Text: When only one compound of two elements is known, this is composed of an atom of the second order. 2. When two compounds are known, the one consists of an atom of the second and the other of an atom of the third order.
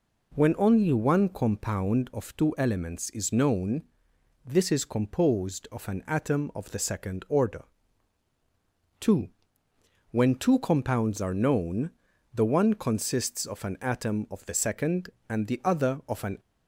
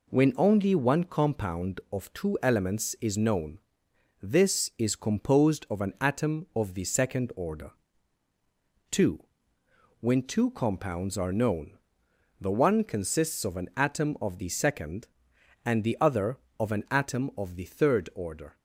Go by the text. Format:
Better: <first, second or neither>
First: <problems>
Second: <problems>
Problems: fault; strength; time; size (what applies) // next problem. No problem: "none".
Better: second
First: stops before "atom of the third order"; at 16.3 s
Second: none